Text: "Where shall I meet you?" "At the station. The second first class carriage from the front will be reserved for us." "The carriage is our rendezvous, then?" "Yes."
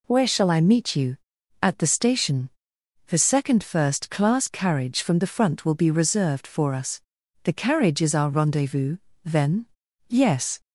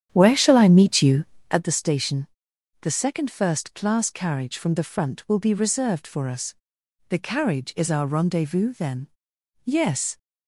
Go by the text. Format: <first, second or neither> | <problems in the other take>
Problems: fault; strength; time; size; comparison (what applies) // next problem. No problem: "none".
first | starts louder than the rest; strong; until 1.7 s; 9.5 dB